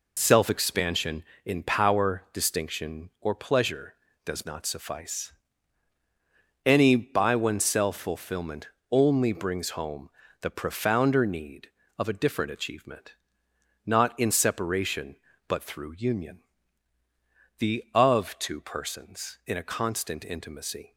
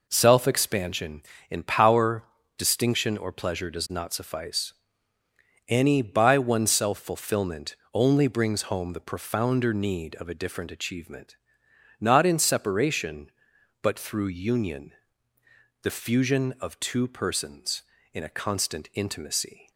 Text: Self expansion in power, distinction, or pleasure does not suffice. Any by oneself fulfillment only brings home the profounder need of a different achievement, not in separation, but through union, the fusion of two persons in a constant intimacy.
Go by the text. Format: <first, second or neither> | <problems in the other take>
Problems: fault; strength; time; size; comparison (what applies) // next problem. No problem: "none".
second | pauses between "fulfillment" and "only"; slight; at 8.6 s; 0.22 s long; slight in the second // pauses between "home" and "the"; slight; at 10.0 s; 0.32 s long // skips "fusion"; at 17.8 s